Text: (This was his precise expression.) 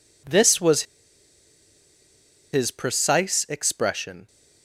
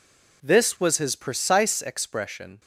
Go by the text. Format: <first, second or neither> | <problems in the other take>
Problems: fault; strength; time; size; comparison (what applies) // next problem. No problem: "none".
second | pauses between "was" and "his"; strong; at 0.8 s; 1.6 s long